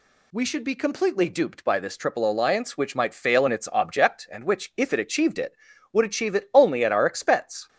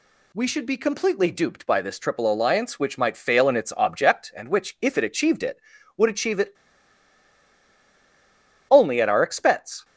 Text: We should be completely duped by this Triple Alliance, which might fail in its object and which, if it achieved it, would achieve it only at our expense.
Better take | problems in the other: first | pauses between "it" and "only"; strong; at 6.5 s; 2.1 s long

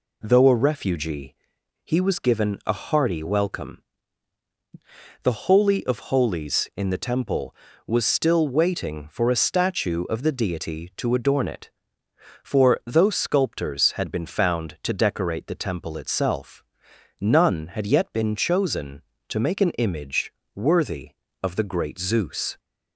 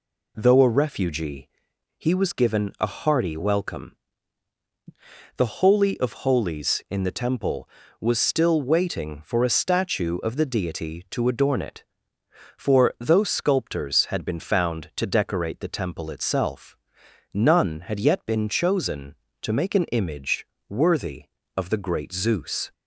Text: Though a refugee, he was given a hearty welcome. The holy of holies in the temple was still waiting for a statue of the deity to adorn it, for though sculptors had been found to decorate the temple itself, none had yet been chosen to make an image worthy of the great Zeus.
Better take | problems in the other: neither | pauses between "image" and "worthy"; slight; the same in both

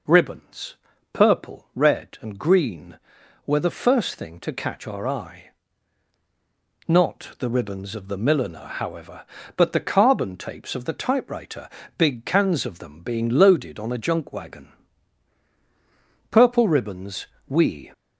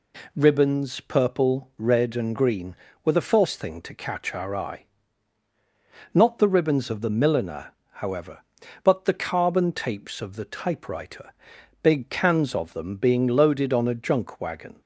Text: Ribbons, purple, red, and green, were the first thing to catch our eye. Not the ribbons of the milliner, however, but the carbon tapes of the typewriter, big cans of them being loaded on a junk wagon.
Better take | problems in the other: second | goes on to say "Purple Ribbons we"; from 16.2 s on; 1.6 s long

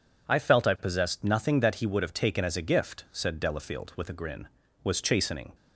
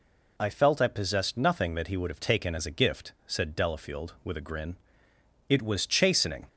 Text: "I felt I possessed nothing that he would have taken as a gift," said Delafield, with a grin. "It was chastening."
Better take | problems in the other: second | skips "It"; at 4.6 s

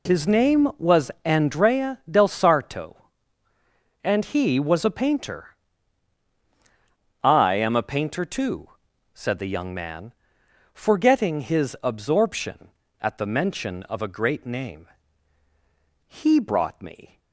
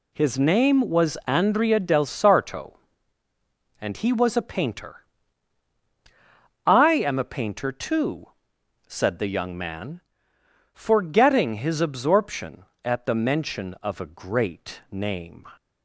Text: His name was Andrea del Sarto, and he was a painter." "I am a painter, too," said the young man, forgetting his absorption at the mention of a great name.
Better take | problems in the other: second | goes on to say "He brought me"; noticeable; from 16.0 s on; 1.1 s long

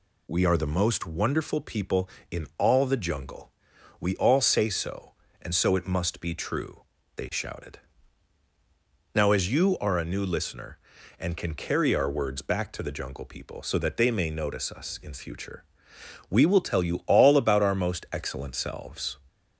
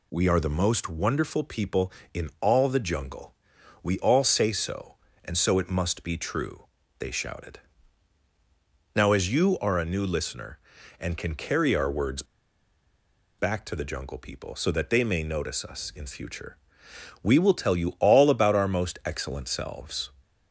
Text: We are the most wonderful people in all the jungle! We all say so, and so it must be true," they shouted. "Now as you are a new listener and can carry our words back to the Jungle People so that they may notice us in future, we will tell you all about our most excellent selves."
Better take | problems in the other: first | pauses between "words" and "back"; at 12.2 s; 1.1 s long

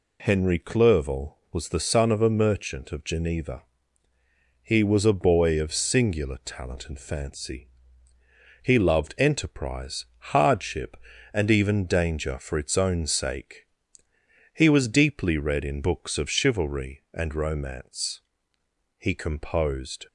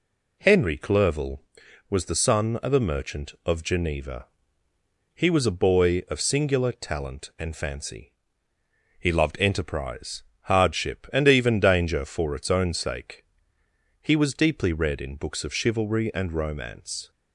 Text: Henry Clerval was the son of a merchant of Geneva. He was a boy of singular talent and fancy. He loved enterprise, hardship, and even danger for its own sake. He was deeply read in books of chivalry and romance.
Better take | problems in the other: second | goes on to say "He composed"; noticeable; from 18.9 s on; 1.0 s long

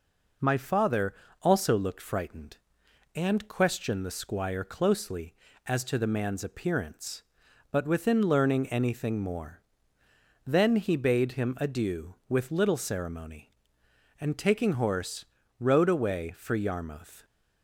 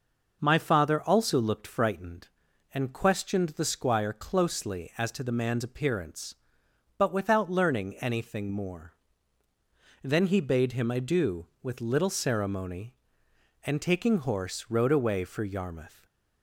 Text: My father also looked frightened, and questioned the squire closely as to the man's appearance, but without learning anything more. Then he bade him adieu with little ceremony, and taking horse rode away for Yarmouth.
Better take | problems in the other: second | pauses between "father" and "also"; slight; at 1.1 s; 0.28 s long // says "within" for "without"; at 7.8 s // pauses between "horse" and "rode"; slight; at 15.2 s; 0.34 s long

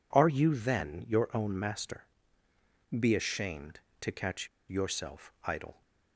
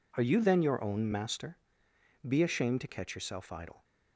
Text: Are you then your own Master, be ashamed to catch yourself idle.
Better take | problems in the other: second | pauses between "catch" and "yourself"; slight; at 4.4 s; 0.21 s long

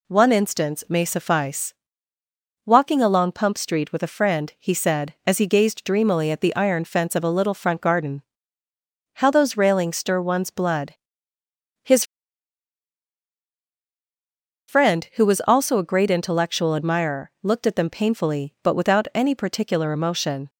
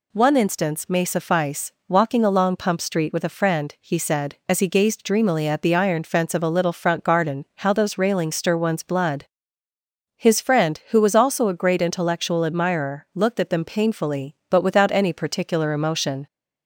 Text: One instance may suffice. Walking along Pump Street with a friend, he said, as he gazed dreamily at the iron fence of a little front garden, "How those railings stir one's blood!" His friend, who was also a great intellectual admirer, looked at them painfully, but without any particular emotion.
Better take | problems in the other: second | pauses between "His" and "friend"; strong; at 12.0 s; 2.6 s long

